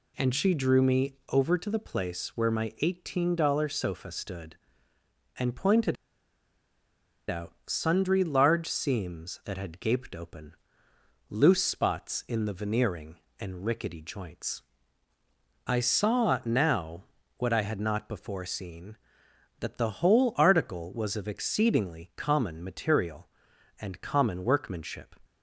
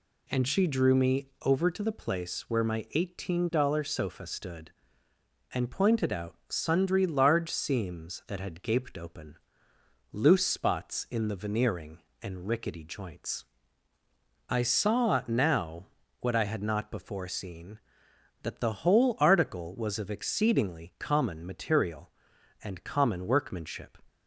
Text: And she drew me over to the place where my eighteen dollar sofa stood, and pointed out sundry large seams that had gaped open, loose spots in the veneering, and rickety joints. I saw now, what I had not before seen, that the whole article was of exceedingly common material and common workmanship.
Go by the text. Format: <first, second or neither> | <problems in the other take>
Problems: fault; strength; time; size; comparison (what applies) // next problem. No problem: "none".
second | pauses between "me" and "over"; slight; at 1.1 s; 0.16 s long; slight in the second // pauses between "pointed" and "out"; strong; at 5.9 s; 1.3 s long